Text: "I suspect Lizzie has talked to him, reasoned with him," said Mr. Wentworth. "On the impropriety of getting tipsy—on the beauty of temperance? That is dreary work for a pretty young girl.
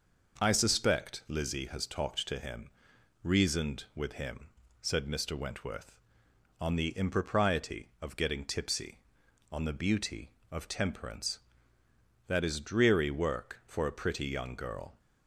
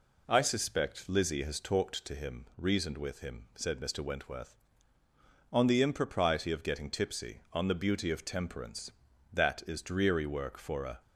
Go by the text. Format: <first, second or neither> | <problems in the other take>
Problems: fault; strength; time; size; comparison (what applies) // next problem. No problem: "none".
first | stops before "pretty young girl"; at 11.0 s